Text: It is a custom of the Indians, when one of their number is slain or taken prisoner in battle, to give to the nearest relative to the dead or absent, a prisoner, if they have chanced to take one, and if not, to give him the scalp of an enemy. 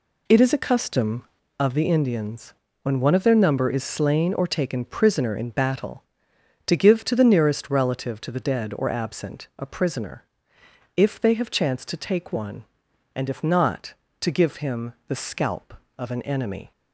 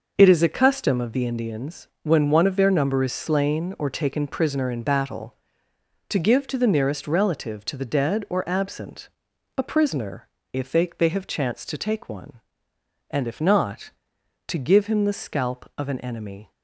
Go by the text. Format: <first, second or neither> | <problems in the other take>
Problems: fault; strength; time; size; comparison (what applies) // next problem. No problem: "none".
first | says "they" twice; at 10.9 s